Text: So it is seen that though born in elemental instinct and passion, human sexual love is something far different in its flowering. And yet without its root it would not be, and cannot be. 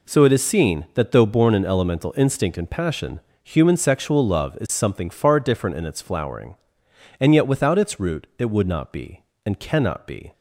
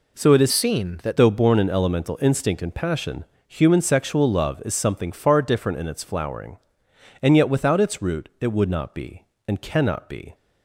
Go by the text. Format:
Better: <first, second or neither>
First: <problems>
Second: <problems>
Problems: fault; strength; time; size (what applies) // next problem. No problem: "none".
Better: first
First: none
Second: changes voice from "seen" to "that"; from 0.5 to 1.1 s; 0.6 s long